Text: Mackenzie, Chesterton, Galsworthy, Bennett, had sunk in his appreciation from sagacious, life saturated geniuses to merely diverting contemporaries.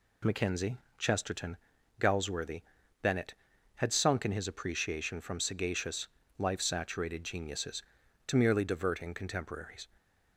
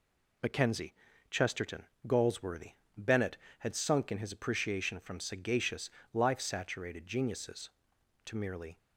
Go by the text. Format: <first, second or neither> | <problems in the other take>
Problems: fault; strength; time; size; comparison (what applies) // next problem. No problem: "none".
first | stops before "diverting contemporaries"; at 8.7 s